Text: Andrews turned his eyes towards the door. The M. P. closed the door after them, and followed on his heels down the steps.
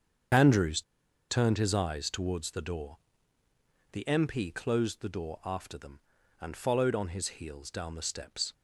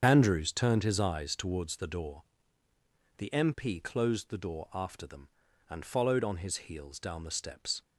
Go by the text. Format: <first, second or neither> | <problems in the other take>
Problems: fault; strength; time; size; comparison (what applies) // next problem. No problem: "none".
second | starts louder than the rest; strong; until 1.8 s; 7.5 dB; strong in the second // pauses between "Andrews" and "turned"; noticeable; at 0.8 s; 0.48 s long